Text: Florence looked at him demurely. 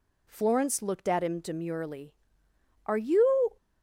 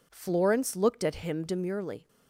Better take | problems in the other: second | goes on to say "Are you"; noticeable; from 2.8 s on; 0.72 s long

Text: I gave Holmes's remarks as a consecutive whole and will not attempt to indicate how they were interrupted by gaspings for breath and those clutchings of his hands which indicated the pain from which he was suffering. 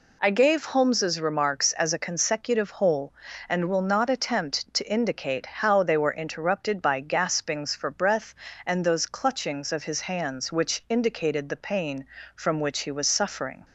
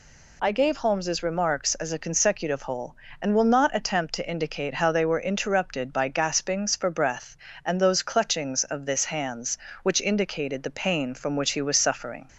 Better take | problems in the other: first | says "this" for "his"; at 8.8 s

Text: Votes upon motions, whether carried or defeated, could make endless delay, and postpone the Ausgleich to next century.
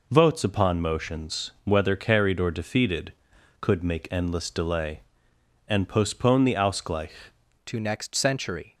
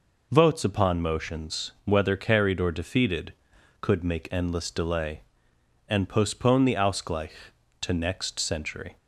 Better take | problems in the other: second | changes voice at "to"; from 7.6 s on; 1.1 s long

